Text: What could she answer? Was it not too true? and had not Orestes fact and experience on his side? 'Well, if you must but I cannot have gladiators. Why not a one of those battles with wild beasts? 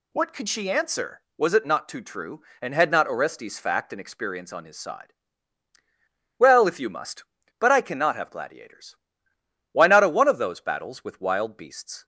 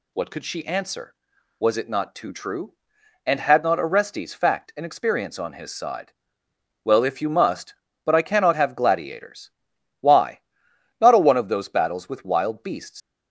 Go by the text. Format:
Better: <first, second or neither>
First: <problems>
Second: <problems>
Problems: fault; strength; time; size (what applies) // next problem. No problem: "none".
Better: first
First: none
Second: pauses between "Why" and "not"; noticeable; at 10.4 s; 0.60 s long // leaves "beasts" unfinished; at 13.0 s; 140 ms